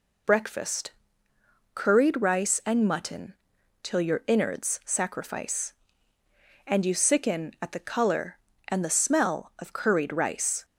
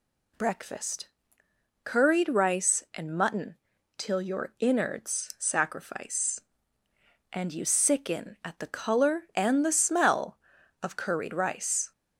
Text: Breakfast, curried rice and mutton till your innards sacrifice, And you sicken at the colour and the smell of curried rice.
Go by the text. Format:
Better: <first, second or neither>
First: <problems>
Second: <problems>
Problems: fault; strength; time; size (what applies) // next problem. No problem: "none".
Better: neither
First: pauses between "mutton" and "till"; noticeable; at 3.3 s; 0.48 s long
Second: pauses between "mutton" and "till"; at 3.5 s; 0.44 s long